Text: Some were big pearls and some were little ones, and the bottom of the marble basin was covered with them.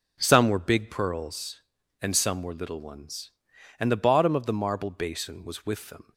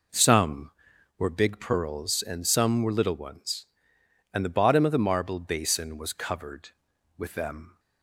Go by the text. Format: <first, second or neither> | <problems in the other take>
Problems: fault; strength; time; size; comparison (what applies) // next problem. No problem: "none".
second | skips "covered"; at 5.6 s